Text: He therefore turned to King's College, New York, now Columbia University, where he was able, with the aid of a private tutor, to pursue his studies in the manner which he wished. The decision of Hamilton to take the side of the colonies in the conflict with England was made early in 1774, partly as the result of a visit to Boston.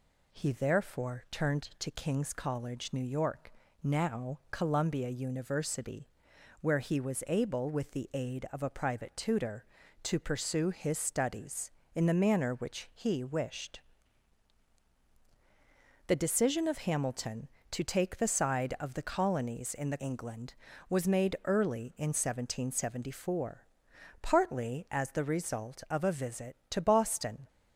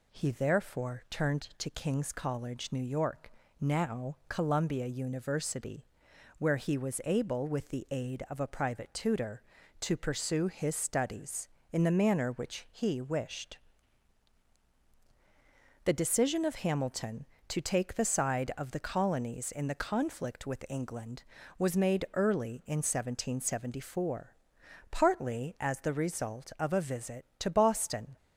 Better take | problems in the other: second | skips "conflict with"; at 19.9 s

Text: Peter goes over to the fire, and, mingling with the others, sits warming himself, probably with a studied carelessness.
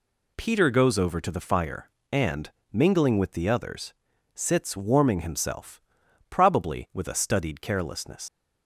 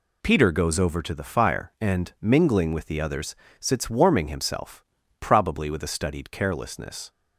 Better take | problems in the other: second | leaves "carelessness" unfinished; at 8.2 s; 100 ms

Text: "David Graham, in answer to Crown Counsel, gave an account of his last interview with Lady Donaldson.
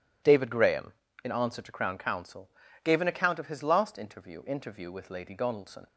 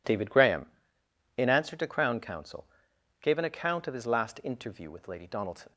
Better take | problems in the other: second | says "interview" twice; at 4.4 s

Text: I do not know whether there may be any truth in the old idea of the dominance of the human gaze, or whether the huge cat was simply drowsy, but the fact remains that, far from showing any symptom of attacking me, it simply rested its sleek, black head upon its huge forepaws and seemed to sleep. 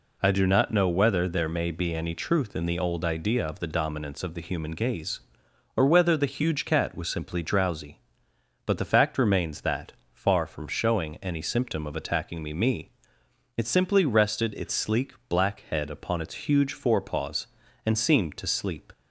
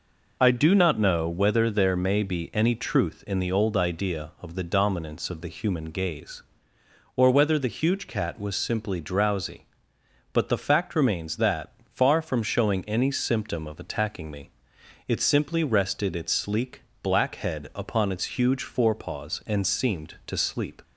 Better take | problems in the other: second | says "me" twice; at 12.5 s

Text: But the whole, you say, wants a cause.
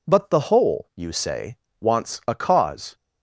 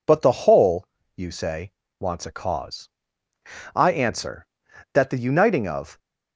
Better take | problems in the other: first | goes on to say "I answer that the uniting of"; strong; from 3.7 s on; 2.2 s long

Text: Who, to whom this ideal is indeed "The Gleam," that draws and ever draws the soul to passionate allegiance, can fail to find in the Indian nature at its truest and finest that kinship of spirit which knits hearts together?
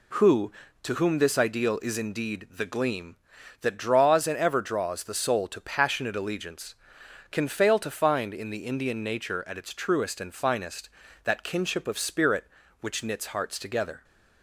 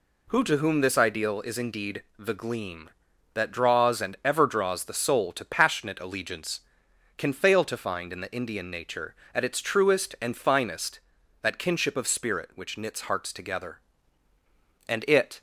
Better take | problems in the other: first | pauses between "indeed" and "The"; slight; at 2.0 s; 0.16 s long // goes on to say "And it"; from 14.8 s on; 0.54 s long

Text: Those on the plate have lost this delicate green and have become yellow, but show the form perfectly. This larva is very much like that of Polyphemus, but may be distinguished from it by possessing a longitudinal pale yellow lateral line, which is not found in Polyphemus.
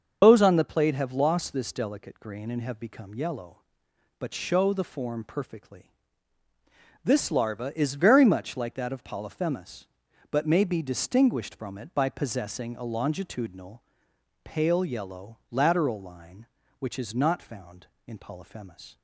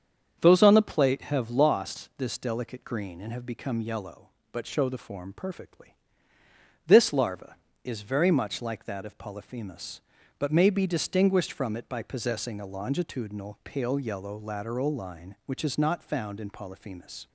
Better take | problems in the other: second | loses the start of "Those"; at 0.2 s; 90 ms // starts louder than the rest; until 1.2 s; 6.5 dB; strong in the second // pauses between "longitudinal" and "pale"; noticeable; at 13.8 s; 0.62 s long

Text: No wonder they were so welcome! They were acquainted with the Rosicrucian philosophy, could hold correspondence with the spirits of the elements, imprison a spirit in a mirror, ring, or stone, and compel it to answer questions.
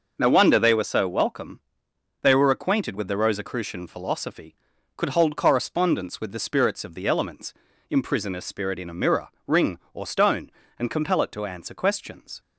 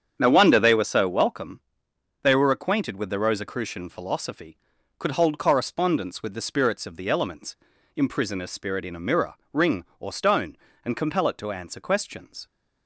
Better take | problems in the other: first | starts louder than the rest; strong; until 1.6 s; 8 dB

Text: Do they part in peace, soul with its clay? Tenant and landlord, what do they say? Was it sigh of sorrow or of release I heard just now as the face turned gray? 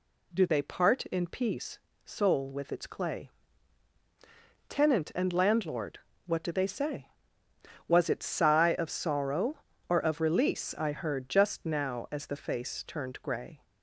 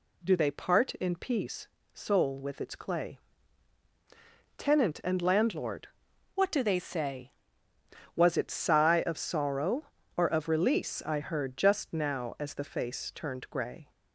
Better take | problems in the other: first | changes voice from "what" to "say"; from 6.3 to 7.3 s; 1.0 s long

